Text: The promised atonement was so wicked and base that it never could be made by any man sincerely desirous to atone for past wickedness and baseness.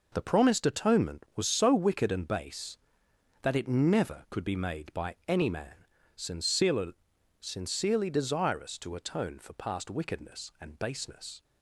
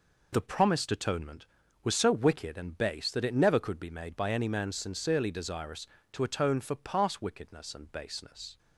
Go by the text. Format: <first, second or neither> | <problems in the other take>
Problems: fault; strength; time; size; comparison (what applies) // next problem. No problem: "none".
second | pauses between "man" and "sincerely"; slight; at 5.8 s; 0.28 s long // says "sincerely" twice; at 7.4 s